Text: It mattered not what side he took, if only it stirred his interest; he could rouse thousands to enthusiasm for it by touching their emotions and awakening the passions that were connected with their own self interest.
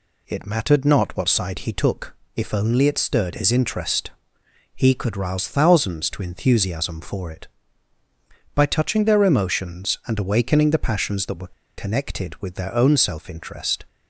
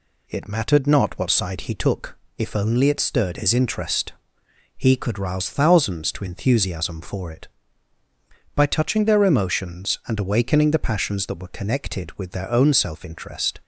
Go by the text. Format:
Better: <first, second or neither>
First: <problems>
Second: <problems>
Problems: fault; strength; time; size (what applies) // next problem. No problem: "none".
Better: second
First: pauses between "were" and "connected"; slight; at 11.5 s; 0.25 s long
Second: none